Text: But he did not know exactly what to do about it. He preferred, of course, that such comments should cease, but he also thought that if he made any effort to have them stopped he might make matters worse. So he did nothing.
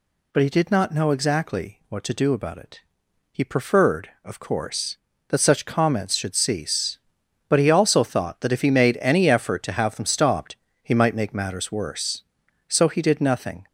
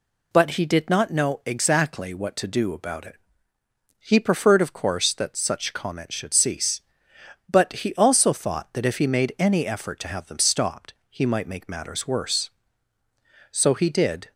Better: first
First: pauses between "stopped" and "he"; slight; at 10.5 s; 0.28 s long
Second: pauses between "stopped" and "he"; slight; at 10.9 s; 0.20 s long // stops before "nothing"; at 14.3 s

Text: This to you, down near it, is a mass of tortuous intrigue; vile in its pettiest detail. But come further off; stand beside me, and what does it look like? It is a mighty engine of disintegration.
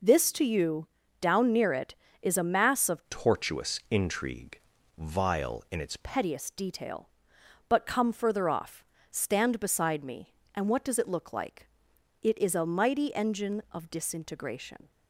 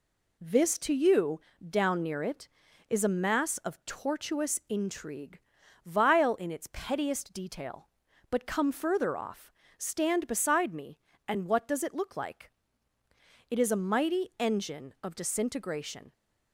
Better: second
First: changes voice from "tortuous" to "its"; from 3.0 to 5.9 s; 2.9 s long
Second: none

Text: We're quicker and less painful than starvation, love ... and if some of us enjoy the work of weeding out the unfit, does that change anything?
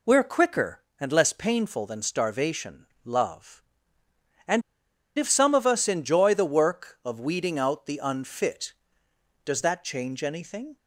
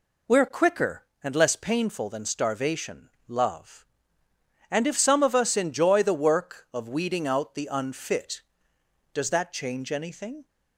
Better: second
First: pauses between "and" and "if"; noticeable; at 4.6 s; 0.57 s long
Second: none

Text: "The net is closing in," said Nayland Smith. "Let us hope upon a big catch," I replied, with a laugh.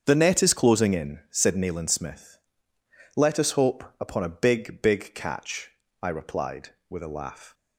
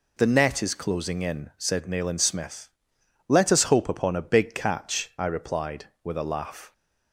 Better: second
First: starts louder than the rest; strong; until 1.0 s; 7 dB // pauses between "hope" and "upon"; slight; at 3.8 s; 0.16 s long // says "big" twice; at 4.8 s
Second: none

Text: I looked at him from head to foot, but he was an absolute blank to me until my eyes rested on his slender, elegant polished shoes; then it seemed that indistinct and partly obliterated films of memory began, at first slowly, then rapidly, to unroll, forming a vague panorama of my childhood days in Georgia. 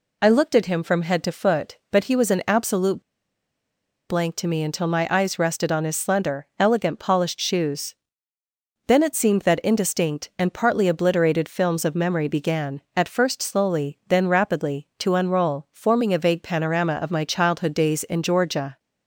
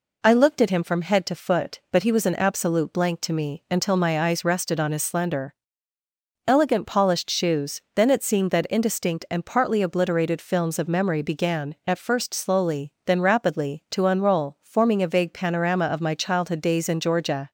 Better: second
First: pauses between "absolute" and "blank"; at 3.0 s; 1.0 s long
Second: none

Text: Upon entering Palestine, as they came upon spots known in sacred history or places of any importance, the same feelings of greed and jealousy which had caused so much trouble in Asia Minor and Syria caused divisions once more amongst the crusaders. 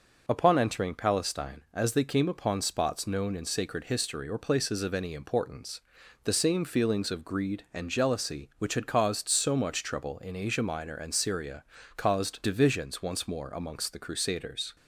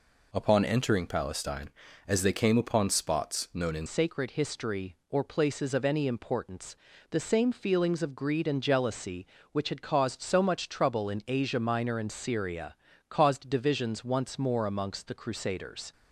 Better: first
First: pauses between "Syria" and "caused"; slight; at 11.6 s; 0.32 s long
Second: changes voice at "sacred"; from 3.8 s on; 12.1 s long // pauses between "Syria" and "caused"; slight; at 12.7 s; 0.36 s long

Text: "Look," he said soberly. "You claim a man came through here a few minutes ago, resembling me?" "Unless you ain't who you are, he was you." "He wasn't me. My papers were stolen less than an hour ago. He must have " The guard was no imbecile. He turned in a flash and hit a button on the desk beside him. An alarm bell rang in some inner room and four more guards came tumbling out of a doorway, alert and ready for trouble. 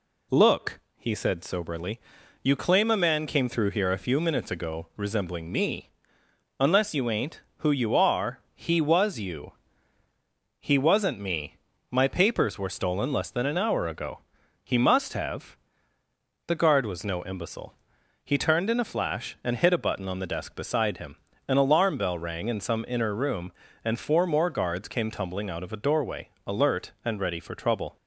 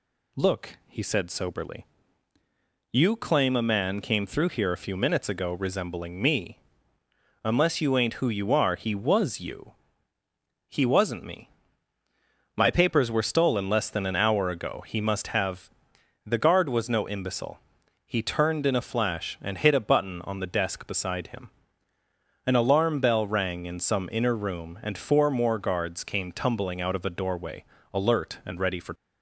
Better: first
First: none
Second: stops before "trouble"; at 28.9 s

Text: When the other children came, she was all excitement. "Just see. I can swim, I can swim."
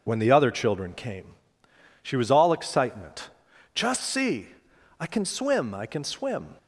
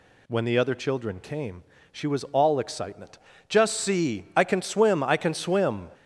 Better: neither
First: none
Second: none

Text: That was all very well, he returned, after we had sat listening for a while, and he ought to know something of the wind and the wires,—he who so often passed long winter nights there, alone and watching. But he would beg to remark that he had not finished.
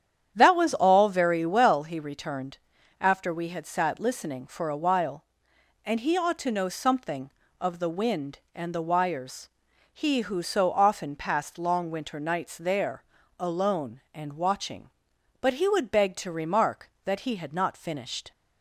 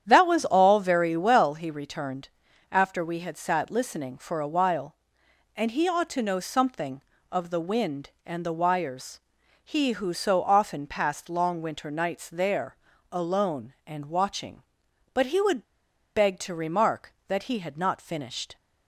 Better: first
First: starts louder than the rest; strong; until 1.3 s; 9 dB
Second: starts louder than the rest; strong; until 1.0 s; 9 dB // pauses between "would" and "beg"; noticeable; at 15.6 s; 0.52 s long

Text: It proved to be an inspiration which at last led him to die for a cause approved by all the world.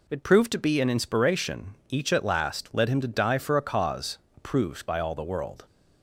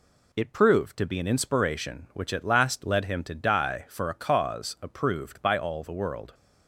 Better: second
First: says "each" for "which"; at 1.8 s // pauses between "cause" and "approved"; slight; at 4.1 s; 0.18 s long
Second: none

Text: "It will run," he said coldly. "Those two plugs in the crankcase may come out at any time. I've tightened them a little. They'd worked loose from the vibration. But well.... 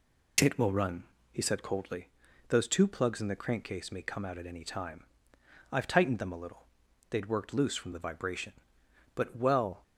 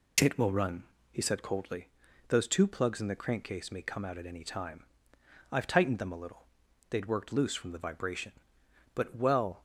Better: neither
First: none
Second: none

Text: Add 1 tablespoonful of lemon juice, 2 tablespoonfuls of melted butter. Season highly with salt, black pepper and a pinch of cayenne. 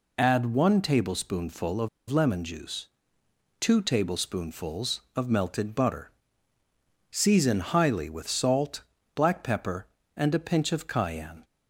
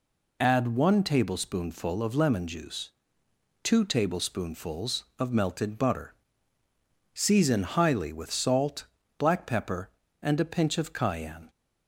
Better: second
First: pauses between "of" and "lemon"; slight; at 1.8 s; 0.21 s long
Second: none

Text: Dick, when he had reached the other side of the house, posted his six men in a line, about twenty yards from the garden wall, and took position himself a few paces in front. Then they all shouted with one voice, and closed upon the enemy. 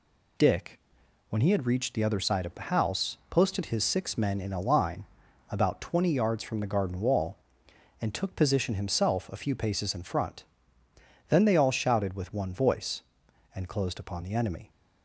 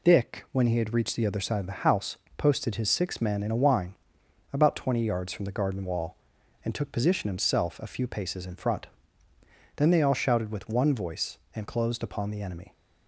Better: first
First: none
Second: says "wine" for "line"; at 3.5 s

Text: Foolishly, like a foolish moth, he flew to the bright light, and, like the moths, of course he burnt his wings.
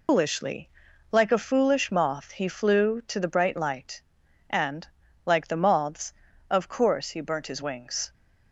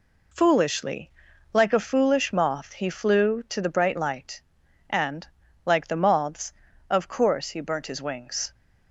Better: second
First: loses the start of "Foolishly"; at 0.0 s; 170 ms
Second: none

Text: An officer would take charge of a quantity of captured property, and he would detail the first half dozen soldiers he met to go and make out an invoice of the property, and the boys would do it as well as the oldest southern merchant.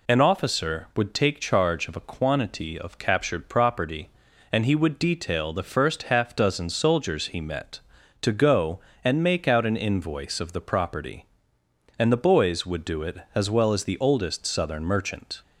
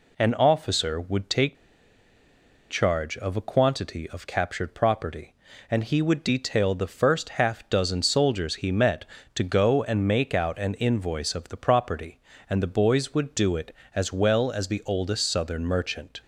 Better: first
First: none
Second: pauses between "take" and "charge"; at 1.5 s; 1.1 s long

